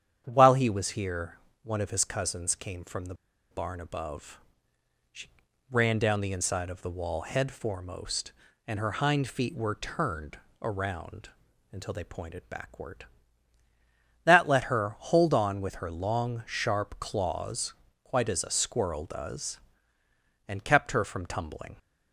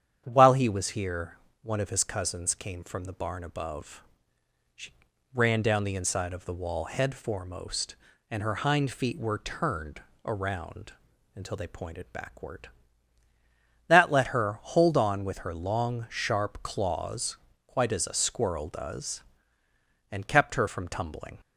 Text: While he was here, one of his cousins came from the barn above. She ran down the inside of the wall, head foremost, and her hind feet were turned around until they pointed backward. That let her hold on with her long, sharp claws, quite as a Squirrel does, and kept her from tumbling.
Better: second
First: starts louder than the rest; strong; until 1.2 s; 9 dB // pauses between "the" and "barn"; at 3.1 s; 0.37 s long // pauses between "She" and "ran"; at 5.2 s; 0.40 s long // pauses between "turned" and "around"; slight; at 10.3 s; 0.22 s long // pauses between "around" and "until"; at 11.2 s; 0.42 s long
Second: starts louder than the rest; strong; until 1.2 s; 9 dB // pauses between "She" and "ran"; at 4.9 s; 0.40 s long // pauses between "turned" and "around"; slight; at 10.0 s; 0.22 s long // pauses between "around" and "until"; at 10.9 s; 0.42 s long

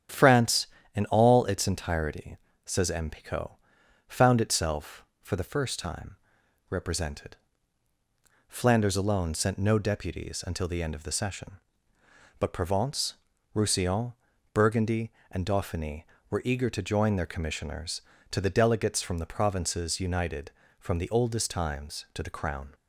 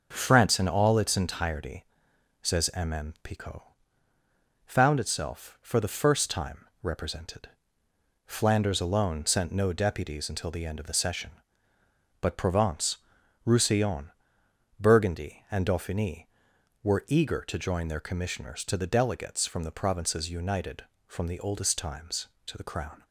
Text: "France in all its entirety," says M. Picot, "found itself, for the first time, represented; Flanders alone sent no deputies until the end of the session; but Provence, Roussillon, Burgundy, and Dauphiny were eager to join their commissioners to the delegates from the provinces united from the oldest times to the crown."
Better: first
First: starts louder than the rest; strong; until 1.3 s; 8.5 dB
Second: starts louder than the rest; strong; until 1.1 s; 7 dB // says "M" twice; at 2.9 s

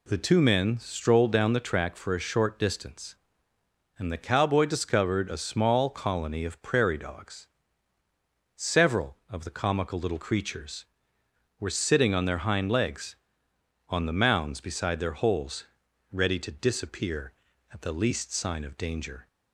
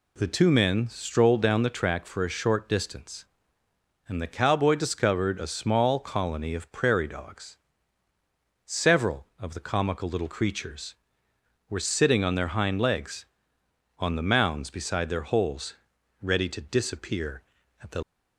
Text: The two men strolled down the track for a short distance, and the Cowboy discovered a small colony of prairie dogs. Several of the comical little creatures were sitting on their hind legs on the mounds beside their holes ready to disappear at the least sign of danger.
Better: first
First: pauses between "holes" and "ready"; noticeable; at 15.6 s; 0.48 s long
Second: pauses between "holes" and "ready"; noticeable; at 15.7 s; 0.48 s long // stops before "least sign of danger"; at 18.0 s

